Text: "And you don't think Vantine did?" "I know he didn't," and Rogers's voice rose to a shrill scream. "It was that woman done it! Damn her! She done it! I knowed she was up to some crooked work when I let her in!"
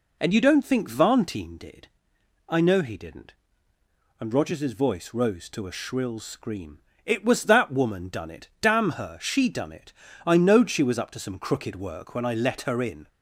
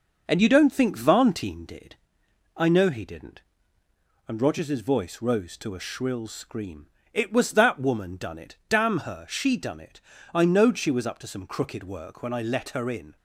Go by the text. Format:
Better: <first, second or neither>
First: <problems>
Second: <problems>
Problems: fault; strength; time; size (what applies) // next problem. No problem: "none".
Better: first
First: none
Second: gets quieter; throughout; 3.5 dB